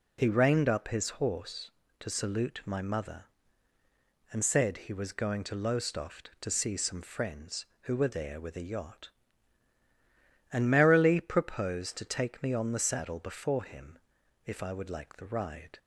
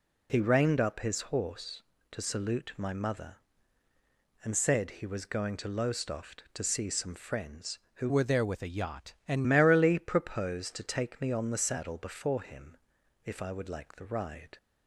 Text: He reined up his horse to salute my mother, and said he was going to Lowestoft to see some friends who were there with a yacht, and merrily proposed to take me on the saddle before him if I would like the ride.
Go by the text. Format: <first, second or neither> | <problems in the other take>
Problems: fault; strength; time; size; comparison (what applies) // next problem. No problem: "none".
first | changes voice from "were" to "and"; from 8.0 to 9.4 s; 1.4 s long // pauses between "him" and "if"; noticeable; at 12.7 s; 0.48 s long; noticeable in the first